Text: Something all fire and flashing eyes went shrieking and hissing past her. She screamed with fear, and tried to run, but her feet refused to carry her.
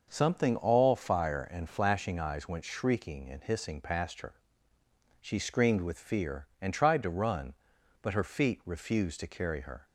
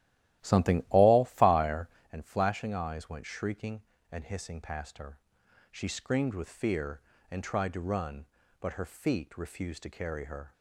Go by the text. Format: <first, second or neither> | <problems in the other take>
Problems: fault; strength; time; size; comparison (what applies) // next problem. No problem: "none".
first | starts louder than the rest; strong; until 2.1 s; 14.5 dB